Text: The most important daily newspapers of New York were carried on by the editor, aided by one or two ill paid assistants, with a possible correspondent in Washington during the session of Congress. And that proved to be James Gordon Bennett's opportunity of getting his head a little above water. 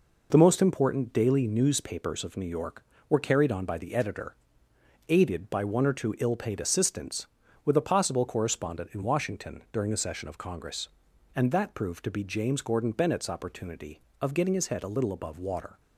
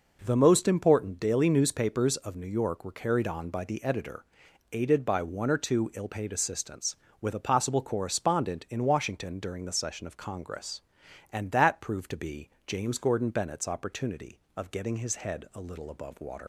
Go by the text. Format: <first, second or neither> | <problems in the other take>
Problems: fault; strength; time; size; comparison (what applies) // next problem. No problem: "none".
first | pauses between "be" and "James"; slight; at 12.4 s; 0.18 s long // leaves "water" unfinished; at 16.4 s; 95 ms